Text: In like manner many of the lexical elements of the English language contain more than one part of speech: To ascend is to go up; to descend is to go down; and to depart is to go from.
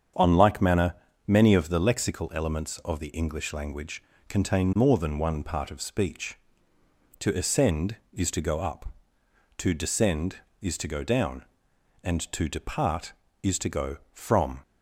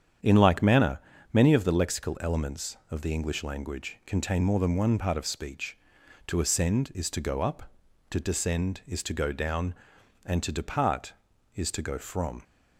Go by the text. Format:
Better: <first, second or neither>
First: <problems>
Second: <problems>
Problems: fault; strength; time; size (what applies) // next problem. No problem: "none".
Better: second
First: starts louder than the rest; strong; until 1.4 s; 7.5 dB // says "On" for "In"; at 0.1 s // pauses between "manner" and "many"; slight; at 0.9 s; 0.32 s long // pauses between "language" and "contain"; slight; at 4.0 s; 0.28 s long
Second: starts louder than the rest; strong; until 1.5 s; 8.5 dB // pauses between "manner" and "many"; slight; at 1.0 s; 0.32 s long